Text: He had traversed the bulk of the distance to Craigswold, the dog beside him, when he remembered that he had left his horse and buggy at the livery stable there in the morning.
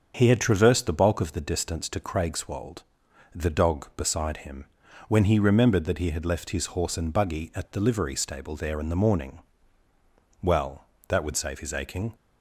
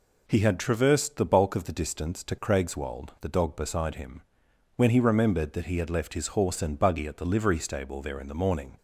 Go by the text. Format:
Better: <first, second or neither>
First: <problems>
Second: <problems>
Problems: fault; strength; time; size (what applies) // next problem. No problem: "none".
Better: second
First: starts louder than the rest; until 1.1 s; 7 dB // goes on to say "Well that would save his aching"; strong; from 10.4 s on; 1.7 s long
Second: none